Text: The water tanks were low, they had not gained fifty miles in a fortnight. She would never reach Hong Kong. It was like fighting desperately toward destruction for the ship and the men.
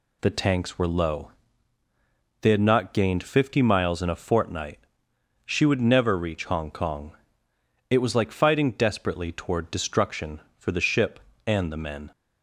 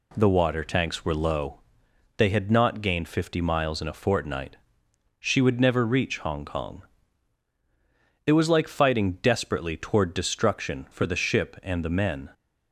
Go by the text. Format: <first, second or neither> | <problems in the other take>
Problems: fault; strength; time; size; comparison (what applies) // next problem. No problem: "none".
second | skips "water"; at 0.2 s